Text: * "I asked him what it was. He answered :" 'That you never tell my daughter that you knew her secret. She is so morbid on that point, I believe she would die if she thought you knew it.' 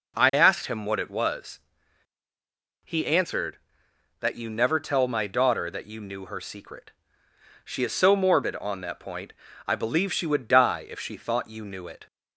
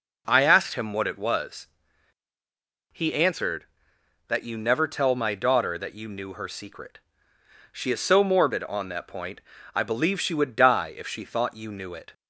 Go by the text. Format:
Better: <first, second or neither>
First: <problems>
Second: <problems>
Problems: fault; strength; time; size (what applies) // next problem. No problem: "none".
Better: neither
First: none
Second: none